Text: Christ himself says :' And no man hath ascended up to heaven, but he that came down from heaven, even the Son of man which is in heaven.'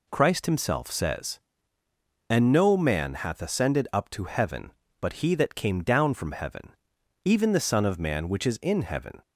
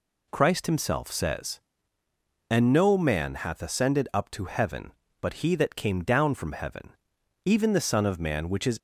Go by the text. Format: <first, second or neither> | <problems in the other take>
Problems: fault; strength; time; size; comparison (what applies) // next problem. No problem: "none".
first | stops before "in heaven"; at 8.7 s